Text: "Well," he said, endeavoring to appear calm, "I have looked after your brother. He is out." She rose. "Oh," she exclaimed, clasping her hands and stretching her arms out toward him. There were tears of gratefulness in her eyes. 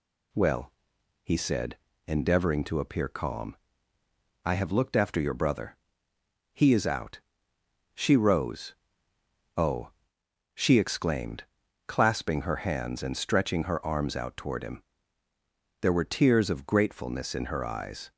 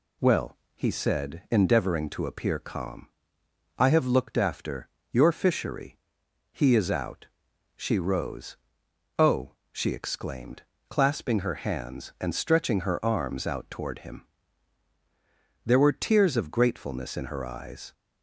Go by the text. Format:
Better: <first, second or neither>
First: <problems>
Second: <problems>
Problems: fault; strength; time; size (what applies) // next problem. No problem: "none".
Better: first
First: none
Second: pauses between "after" and "your"; slight; at 4.8 s; 0.24 s long // says "fishery" for "brother"; at 5.3 s